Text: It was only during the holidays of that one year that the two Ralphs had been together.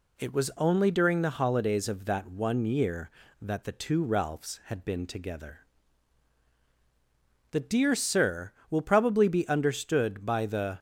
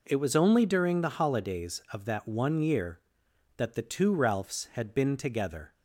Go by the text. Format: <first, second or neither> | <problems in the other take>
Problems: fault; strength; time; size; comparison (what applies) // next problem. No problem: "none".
second | goes on to say "The Dear Sir will probably be understood by the"; strong; from 7.5 s on; 3.2 s long